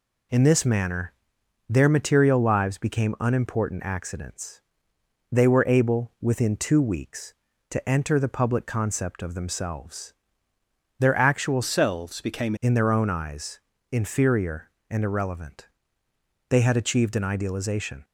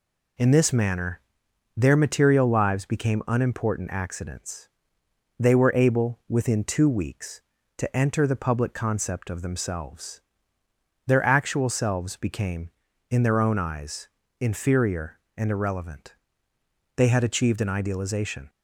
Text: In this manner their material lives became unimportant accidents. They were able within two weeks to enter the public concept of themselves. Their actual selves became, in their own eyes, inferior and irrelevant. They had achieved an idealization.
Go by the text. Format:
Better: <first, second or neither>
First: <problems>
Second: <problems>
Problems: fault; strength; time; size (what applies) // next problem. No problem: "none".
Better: second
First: pauses between "manner" and "their"; noticeable; at 1.1 s; 0.56 s long // changes voice from "selves" to "became"; from 11.6 to 12.5 s; 0.9 s long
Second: pauses between "manner" and "their"; noticeable; at 1.1 s; 0.56 s long